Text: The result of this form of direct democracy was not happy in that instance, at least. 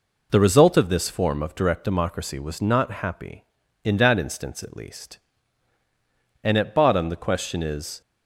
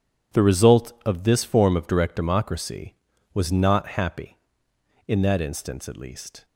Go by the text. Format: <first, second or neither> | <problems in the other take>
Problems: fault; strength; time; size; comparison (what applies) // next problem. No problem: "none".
second | goes on to say "And at bottom the question is"; from 6.4 s on; 1.6 s long